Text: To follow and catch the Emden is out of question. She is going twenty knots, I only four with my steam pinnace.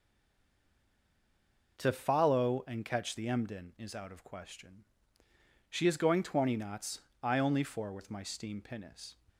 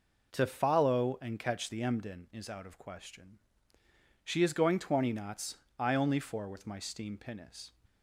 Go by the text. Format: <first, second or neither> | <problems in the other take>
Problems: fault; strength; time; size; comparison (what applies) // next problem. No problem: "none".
second | stays silent before the first word; noticeable; until 1.7 s; 1.7 s long